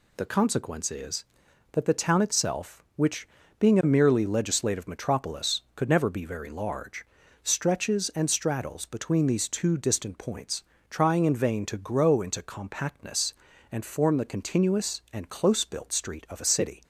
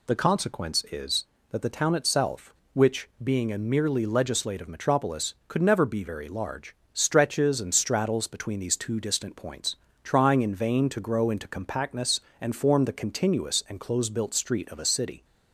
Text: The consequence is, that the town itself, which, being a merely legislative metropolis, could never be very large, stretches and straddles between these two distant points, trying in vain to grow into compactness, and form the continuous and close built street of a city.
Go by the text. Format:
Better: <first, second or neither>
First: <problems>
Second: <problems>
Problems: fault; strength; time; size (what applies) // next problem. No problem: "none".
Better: neither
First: none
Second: none